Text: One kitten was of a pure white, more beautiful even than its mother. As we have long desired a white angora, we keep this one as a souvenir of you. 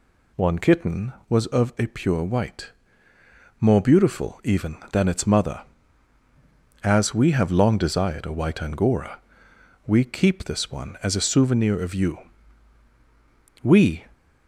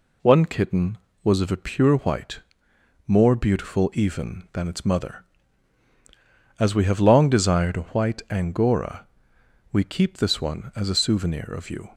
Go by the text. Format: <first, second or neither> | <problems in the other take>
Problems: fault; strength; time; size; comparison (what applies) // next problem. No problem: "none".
second | goes on to say "We"; slight; from 13.6 s on; 0.42 s long